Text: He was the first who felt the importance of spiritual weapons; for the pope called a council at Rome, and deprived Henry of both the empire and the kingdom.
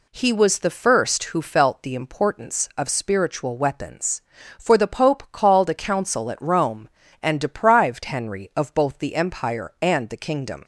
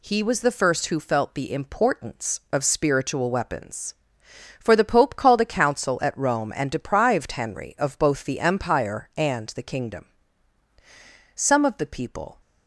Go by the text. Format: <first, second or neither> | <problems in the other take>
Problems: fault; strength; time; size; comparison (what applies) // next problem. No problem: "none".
first | goes on to say "Some of the people"; noticeable; from 11.3 s on; 1.0 s long